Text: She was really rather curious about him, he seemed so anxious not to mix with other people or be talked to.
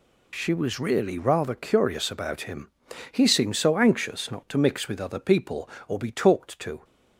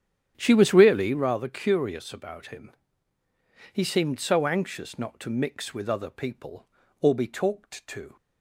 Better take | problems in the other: first | starts louder than the rest; strong; until 1.2 s; 9.5 dB

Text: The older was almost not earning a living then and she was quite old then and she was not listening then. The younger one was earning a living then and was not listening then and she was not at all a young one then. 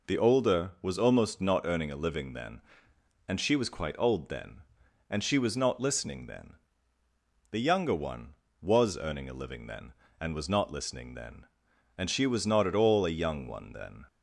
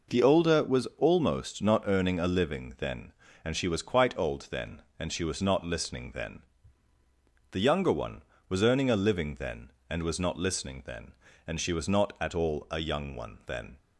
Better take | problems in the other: neither | none

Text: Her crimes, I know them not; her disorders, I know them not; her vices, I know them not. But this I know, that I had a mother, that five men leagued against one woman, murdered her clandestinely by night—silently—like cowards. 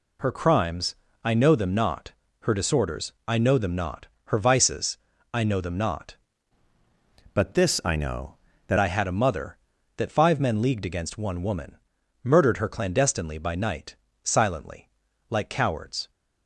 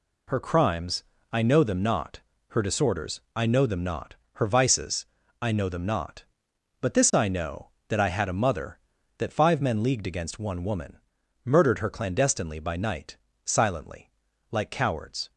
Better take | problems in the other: second | changes voice from "But" to "that"; from 7.3 to 8.7 s; 1.4 s long

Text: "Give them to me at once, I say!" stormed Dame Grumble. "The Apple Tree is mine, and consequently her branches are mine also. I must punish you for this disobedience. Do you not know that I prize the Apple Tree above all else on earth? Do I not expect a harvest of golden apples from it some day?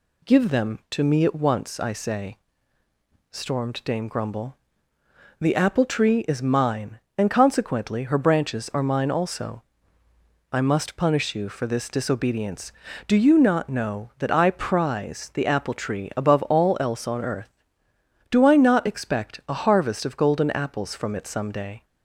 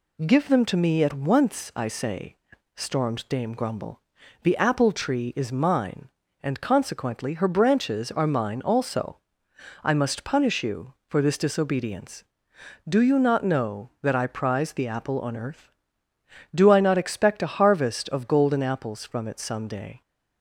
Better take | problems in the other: first | skips "Tree above all else"; at 15.1 s

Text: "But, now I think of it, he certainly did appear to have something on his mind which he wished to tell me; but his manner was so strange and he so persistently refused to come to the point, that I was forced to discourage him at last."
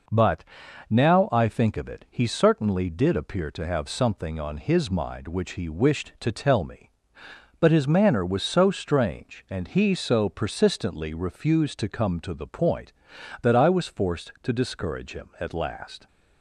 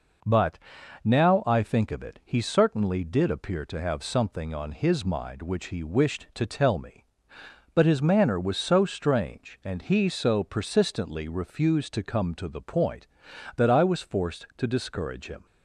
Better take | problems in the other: first | stops before "at last"; at 15.4 s

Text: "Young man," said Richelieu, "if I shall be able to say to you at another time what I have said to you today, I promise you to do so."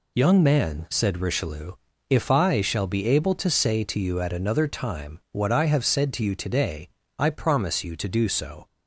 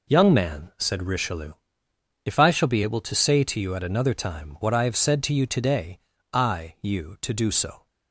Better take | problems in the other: first | skips "promise"; at 6.7 s

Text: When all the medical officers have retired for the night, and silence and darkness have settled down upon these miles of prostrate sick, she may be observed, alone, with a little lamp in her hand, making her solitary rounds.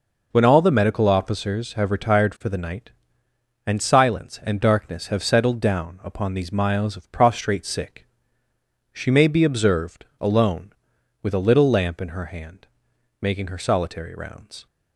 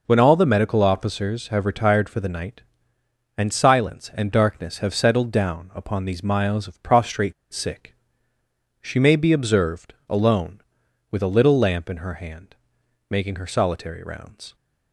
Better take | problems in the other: first | pauses between "prostrate" and "sick"; slight; at 7.3 s; 0.19 s long

